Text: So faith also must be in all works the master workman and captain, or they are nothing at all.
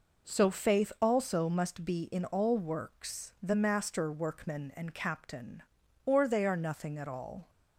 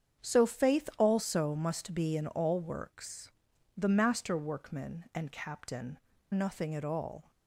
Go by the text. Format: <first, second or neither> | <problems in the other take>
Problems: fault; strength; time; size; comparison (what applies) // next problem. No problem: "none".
first | starts louder than the rest; strong; until 1.3 s; 8 dB // pauses between "works" and "the"; noticeable; at 3.3 s; 0.48 s long // skips "or they are"; at 6.1 s